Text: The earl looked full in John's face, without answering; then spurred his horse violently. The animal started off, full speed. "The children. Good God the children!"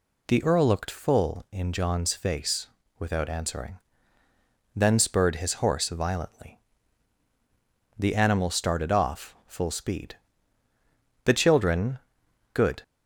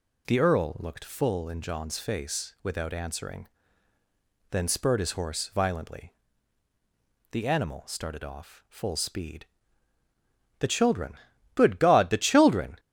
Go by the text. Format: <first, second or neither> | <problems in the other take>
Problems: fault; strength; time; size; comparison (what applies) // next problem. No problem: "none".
second | stops before "God the children"; at 12.8 s